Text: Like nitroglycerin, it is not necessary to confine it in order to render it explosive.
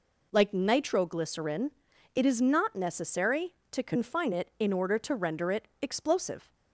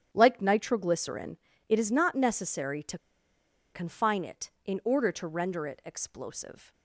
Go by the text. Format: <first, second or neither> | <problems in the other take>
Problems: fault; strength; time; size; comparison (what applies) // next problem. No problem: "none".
first | starts louder than the rest; strong; until 1.1 s; 9.5 dB // pauses between "to" and "confine"; noticeable; at 2.9 s; 0.75 s long